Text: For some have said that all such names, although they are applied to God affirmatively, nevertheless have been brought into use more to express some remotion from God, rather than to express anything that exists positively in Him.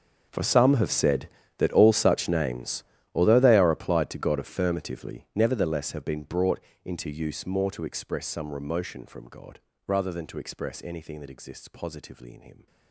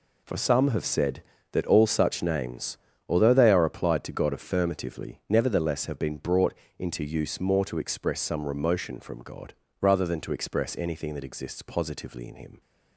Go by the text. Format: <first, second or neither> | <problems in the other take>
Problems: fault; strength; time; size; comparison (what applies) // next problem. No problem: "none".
second | gets quieter; strong; throughout; 19 dB // pauses between "brought" and "into"; slight; at 6.6 s; 0.24 s long; slight in the second